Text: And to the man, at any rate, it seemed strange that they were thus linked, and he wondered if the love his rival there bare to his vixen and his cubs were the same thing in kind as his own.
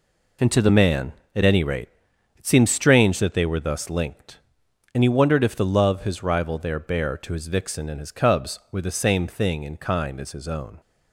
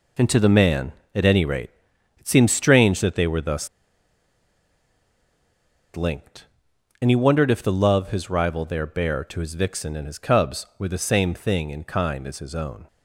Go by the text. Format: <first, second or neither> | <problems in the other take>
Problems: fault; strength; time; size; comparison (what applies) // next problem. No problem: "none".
first | pauses between "thus" and "linked"; strong; at 3.6 s; 2.2 s long